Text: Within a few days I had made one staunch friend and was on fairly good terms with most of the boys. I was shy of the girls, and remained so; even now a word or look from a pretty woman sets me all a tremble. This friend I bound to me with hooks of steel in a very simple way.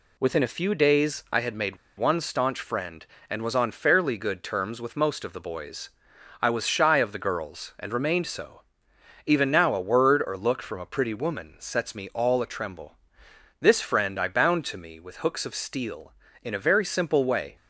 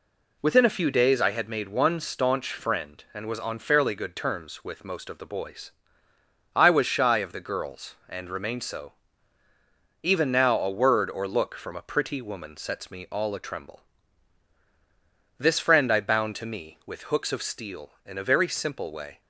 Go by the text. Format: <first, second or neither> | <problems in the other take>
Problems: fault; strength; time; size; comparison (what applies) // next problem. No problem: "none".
second | pauses between "made" and "one"; slight; at 1.7 s; 0.22 s long